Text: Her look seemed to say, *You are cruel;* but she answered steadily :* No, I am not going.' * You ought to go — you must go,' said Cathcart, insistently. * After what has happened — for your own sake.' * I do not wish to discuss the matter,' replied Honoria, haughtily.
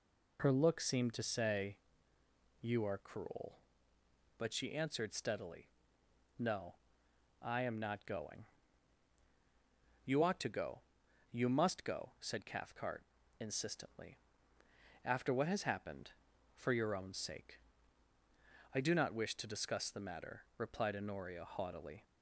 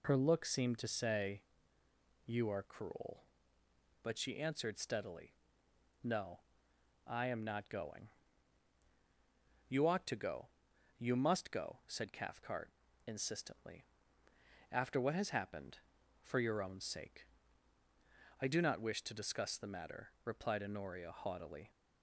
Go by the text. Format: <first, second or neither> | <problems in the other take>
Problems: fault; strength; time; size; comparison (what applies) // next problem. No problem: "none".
neither | none